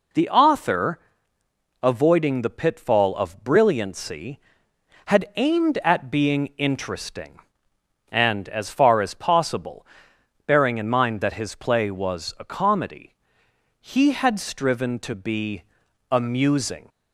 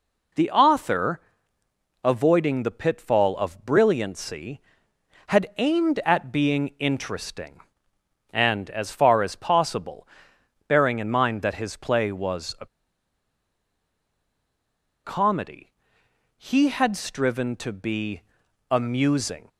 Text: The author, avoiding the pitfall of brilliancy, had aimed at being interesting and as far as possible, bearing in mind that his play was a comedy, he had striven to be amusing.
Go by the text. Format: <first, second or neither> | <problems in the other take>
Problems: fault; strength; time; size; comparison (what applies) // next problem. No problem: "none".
first | pauses between "a" and "comedy"; strong; at 12.6 s; 2.3 s long // pauses between "be" and "amusing"; noticeable; at 18.2 s; 0.48 s long; noticeable in the first